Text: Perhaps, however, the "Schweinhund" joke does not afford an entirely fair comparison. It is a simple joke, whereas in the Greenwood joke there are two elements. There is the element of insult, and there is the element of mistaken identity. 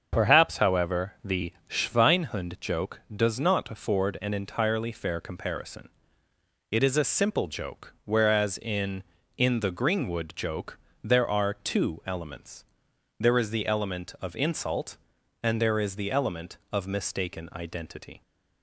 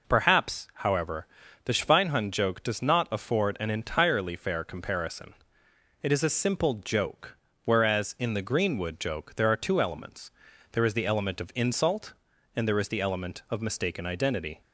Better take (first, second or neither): second